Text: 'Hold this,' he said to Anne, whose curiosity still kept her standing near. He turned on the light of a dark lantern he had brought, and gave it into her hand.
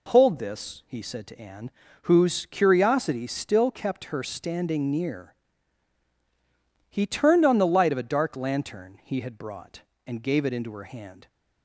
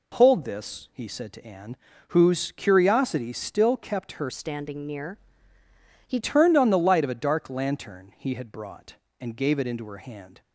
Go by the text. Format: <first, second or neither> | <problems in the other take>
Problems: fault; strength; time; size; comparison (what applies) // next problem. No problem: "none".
first | changes voice from "standing" to "He"; from 4.2 to 6.1 s; 1.9 s long